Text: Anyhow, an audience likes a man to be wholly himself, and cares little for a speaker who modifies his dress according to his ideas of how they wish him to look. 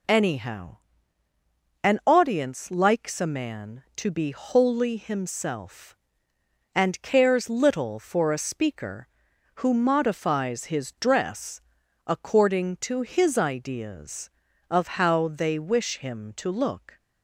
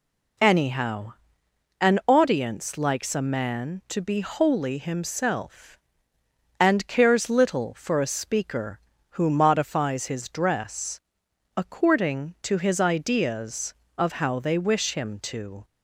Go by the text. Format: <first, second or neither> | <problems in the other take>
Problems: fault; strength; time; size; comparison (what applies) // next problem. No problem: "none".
first | pauses between "dress" and "according"; noticeable; at 10.9 s; 0.56 s long; noticeable in the first // stops before "look"; at 15.6 s